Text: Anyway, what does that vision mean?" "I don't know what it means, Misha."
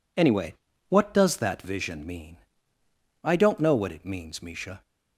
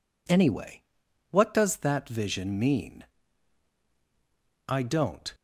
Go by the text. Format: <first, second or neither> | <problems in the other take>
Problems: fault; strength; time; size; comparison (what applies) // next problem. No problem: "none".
first | stops before "know what it means Misha"; at 5.3 s